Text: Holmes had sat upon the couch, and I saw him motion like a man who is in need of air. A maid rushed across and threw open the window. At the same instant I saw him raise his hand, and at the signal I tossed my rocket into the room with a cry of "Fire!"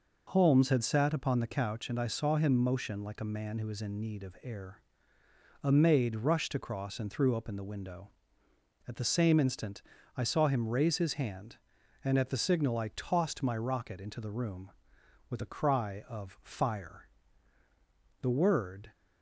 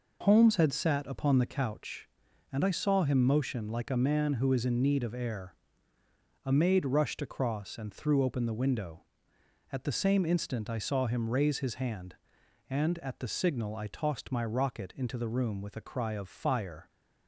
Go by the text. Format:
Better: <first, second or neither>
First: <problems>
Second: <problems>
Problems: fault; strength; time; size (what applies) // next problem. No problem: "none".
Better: second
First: pauses between "instant" and "I"; at 9.8 s; 0.38 s long // goes on to say "The word"; noticeable; from 18.2 s on; 0.70 s long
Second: none